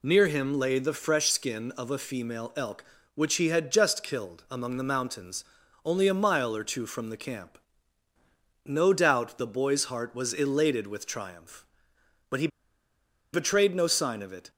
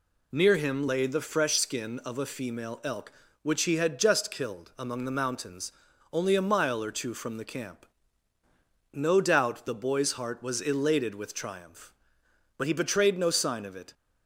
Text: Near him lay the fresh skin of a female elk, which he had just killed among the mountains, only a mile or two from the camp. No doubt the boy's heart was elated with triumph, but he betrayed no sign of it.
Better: second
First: pauses between "he" and "betrayed"; noticeable; at 12.4 s; 0.85 s long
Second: none

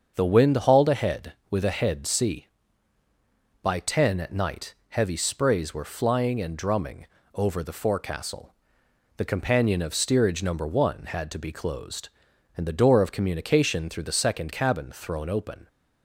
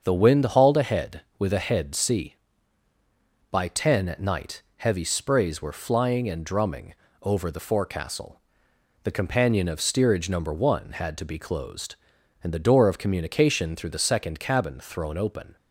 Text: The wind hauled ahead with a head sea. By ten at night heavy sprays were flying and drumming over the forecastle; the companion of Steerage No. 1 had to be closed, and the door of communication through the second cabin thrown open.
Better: neither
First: starts louder than the rest; until 1.1 s; 7 dB // pauses between "night" and "heavy"; slight; at 4.7 s; 0.16 s long // pauses between "drumming" and "over"; slight; at 7.0 s; 0.30 s long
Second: starts louder than the rest; until 1.0 s; 7 dB // pauses between "night" and "heavy"; slight; at 4.6 s; 0.16 s long // pauses between "drumming" and "over"; slight; at 6.9 s; 0.30 s long

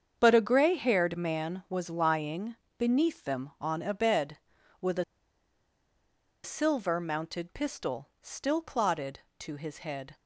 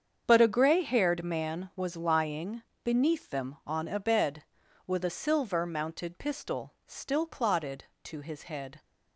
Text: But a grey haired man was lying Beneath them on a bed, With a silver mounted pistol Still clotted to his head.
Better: second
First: starts louder than the rest; strong; until 1.1 s; 7.5 dB // pauses between "lying" and "Beneath"; slight; at 2.5 s; 0.22 s long // pauses between "a" and "silver"; strong; at 5.0 s; 1.4 s long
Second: starts louder than the rest; strong; until 1.2 s; 7.5 dB // pauses between "lying" and "Beneath"; slight; at 2.6 s; 0.21 s long

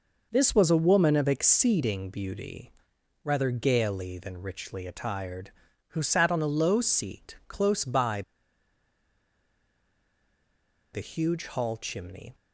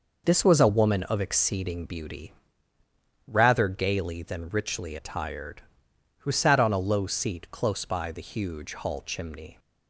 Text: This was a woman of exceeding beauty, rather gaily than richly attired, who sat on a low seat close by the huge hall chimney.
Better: second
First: pauses between "by" and "the"; strong; at 8.2 s; 2.7 s long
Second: none

